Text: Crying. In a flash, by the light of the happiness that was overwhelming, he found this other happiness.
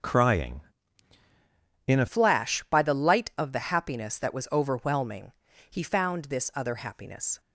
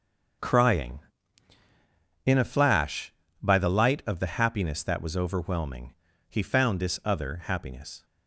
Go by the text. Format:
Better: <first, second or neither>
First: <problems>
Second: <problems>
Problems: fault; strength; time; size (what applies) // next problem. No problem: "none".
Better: second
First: starts louder than the rest; noticeable; until 2.2 s; 6 dB // changes voice at "flash"; from 2.0 s on; 5.3 s long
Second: starts louder than the rest; until 2.6 s; 6.5 dB